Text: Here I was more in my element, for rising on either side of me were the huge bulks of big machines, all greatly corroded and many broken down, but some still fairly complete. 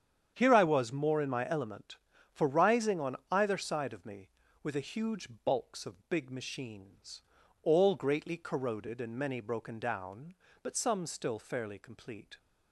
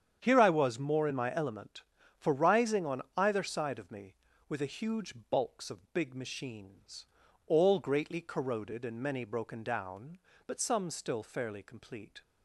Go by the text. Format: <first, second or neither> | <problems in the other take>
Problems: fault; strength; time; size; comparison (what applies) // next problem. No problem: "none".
neither | starts louder than the rest; strong; the same in both // pauses between "huge" and "bulks"; slight; the same in both